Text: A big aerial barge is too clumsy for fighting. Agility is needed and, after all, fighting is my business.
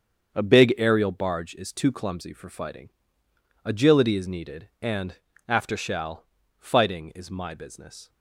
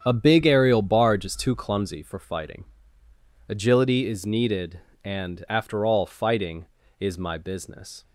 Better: second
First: starts louder than the rest; strong; until 1.3 s; 7.5 dB // says "shall" for "all"; at 5.7 s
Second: starts louder than the rest; strong; until 1.0 s; 8 dB

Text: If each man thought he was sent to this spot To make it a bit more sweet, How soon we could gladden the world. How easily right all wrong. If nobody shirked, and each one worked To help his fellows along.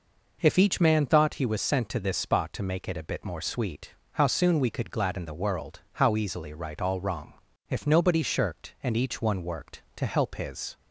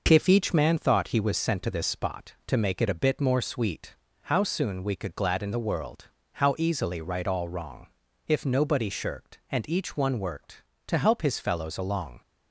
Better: second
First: stops before "fellows along"; at 10.7 s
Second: none

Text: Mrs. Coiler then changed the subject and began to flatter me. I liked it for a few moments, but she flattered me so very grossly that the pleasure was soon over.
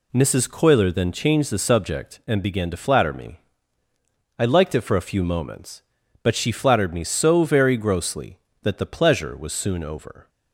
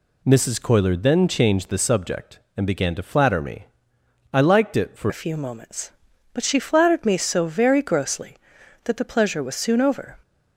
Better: first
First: none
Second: changes voice at "a"; from 5.0 s on; 5.1 s long

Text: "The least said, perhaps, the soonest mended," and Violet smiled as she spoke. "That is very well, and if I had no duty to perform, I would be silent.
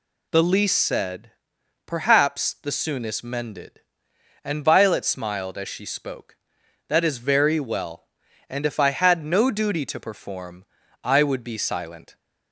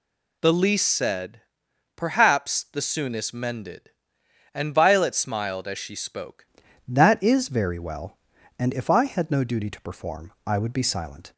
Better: first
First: none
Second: changes voice at "That"; from 6.8 s on; 4.5 s long

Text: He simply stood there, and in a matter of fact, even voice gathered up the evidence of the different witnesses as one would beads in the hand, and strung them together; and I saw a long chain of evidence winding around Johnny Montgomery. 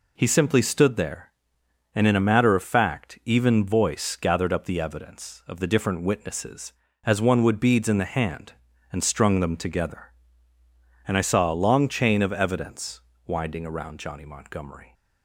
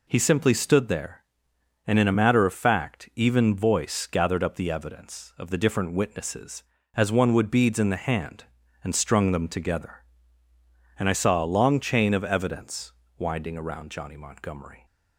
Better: neither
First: pauses between "evidence" and "winding"; slight; at 13.0 s; 0.24 s long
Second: pauses between "evidence" and "winding"; slight; at 12.9 s; 0.24 s long

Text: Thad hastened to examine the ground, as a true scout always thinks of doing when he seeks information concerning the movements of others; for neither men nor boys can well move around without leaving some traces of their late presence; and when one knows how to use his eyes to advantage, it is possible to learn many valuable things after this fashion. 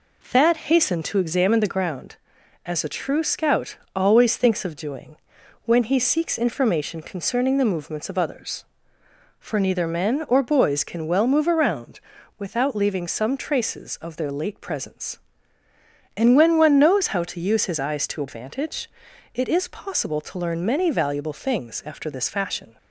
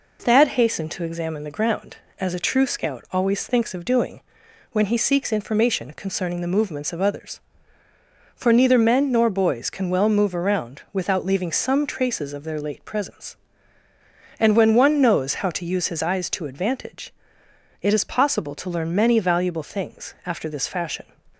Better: second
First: pauses between "scout" and "always"; slight; at 3.7 s; 0.18 s long // pauses between "doing" and "when"; noticeable; at 5.1 s; 0.48 s long // says "or" for "nor"; at 10.2 s // pauses between "around" and "without"; at 11.9 s; 0.40 s long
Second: pauses between "doing" and "when"; noticeable; at 4.2 s; 0.50 s long

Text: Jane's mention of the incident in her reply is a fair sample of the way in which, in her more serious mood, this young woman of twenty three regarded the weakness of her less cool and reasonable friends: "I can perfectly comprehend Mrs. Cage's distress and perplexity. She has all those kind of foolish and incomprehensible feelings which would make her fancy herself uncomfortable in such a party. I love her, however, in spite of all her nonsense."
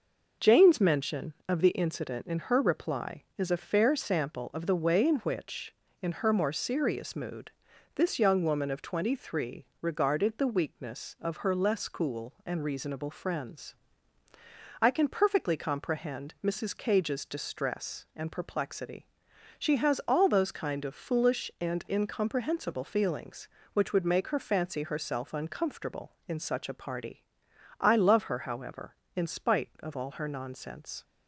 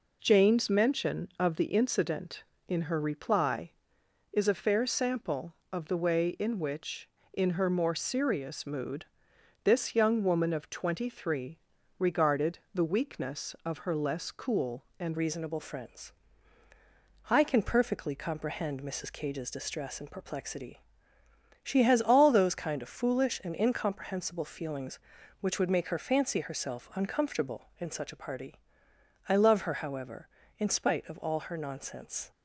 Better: first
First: pauses between "three" and "regarded"; slight; at 9.6 s; 0.16 s long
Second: pauses between "three" and "regarded"; at 11.5 s; 0.42 s long // pauses between "regarded" and "the"; slight; at 12.5 s; 0.16 s long // changes voice at "reasonable"; from 15.1 s on; 17.2 s long

